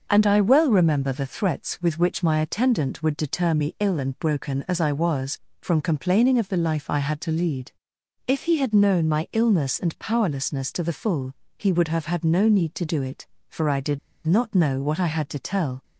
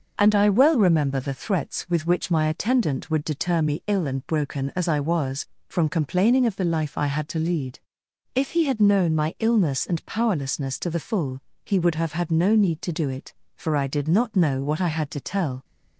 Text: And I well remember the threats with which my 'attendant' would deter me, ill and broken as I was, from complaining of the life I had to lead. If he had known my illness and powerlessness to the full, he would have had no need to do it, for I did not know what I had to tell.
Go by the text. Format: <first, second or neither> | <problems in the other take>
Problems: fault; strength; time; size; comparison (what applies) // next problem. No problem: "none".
second | starts louder than the rest; noticeable; until 1.0 s; 6 dB; noticeable in the second // pauses between "did" and "not"; slight; at 13.9 s; 0.25 s long